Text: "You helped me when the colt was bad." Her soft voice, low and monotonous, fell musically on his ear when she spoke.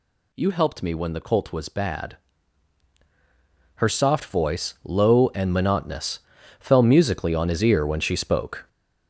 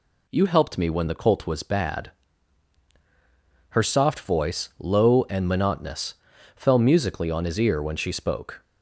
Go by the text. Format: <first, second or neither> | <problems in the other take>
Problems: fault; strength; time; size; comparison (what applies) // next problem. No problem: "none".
second | gets louder; noticeable; throughout; 6 dB